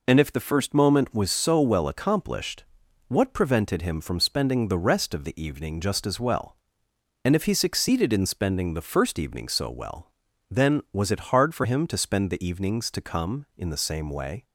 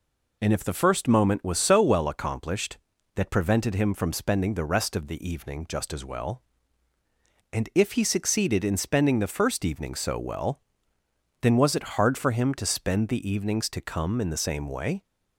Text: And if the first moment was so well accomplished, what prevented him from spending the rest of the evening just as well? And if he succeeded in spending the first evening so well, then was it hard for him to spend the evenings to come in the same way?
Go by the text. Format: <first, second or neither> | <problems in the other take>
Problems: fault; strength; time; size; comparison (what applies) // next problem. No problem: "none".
first | says "that" for "what"; at 3.1 s